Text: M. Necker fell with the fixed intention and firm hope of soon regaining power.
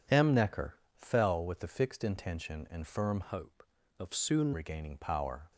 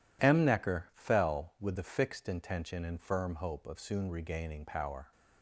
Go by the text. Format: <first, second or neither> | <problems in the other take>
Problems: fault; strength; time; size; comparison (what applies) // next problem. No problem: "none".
second | pauses between "Necker" and "fell"; slight; at 0.7 s; 0.18 s long // changes voice from "hope" to "soon"; from 3.2 to 4.5 s; 1.3 s long